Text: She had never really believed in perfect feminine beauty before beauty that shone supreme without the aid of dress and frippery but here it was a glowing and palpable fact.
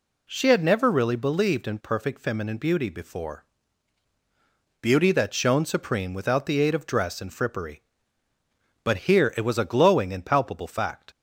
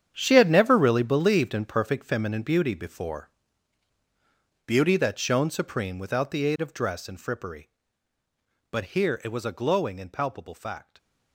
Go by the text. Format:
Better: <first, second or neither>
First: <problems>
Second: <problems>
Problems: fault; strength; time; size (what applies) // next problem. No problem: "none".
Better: first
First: pauses between "before" and "beauty"; strong; at 3.4 s; 1.3 s long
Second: gets quieter; strong; throughout; 13 dB // pauses between "before" and "beauty"; strong; at 3.2 s; 1.3 s long